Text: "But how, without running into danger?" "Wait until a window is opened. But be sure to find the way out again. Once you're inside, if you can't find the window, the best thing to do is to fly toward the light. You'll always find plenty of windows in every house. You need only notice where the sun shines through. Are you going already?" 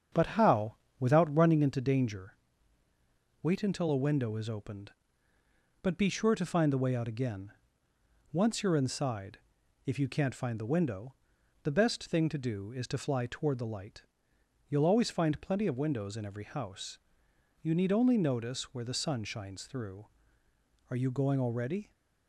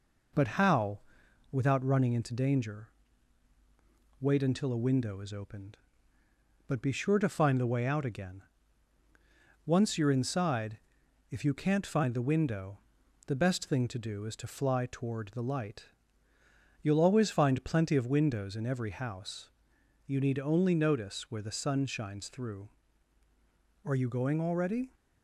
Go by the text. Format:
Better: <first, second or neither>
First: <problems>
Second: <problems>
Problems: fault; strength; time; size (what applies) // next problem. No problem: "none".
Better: second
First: starts louder than the rest; strong; until 1.8 s; 7.5 dB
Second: none